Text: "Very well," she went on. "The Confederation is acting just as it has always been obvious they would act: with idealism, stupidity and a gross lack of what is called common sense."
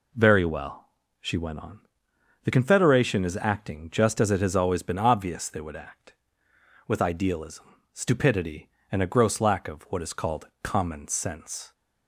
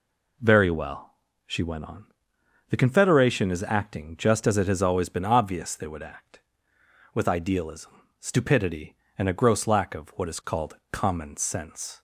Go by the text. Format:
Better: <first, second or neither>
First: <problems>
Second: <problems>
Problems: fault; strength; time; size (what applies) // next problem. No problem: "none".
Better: neither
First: pauses between "called" and "common"; slight; at 10.4 s; 0.16 s long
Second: pauses between "called" and "common"; slight; at 10.7 s; 0.16 s long